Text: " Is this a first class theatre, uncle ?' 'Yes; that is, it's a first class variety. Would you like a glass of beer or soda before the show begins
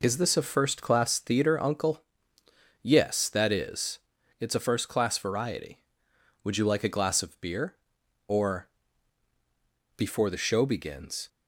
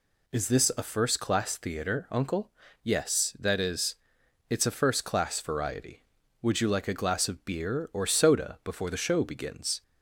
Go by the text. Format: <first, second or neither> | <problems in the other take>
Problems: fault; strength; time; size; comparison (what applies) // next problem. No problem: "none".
second | skips "soda"; at 9.3 s